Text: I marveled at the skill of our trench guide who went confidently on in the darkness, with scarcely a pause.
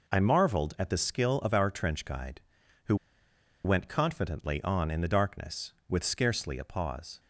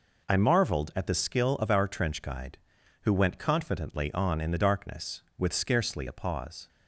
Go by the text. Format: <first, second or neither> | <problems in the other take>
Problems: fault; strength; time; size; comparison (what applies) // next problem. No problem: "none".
second | pauses between "who" and "went"; noticeable; at 2.9 s; 0.69 s long